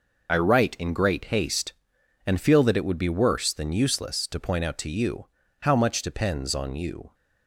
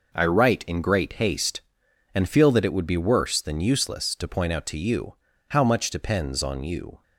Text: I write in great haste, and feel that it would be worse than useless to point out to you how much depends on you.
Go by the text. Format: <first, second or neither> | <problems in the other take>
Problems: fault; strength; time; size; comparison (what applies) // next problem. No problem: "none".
second | loses the start of "I"; at 0.2 s; 40 ms // pauses between "you" and "how"; slight; at 5.2 s; 0.36 s long; slight in the second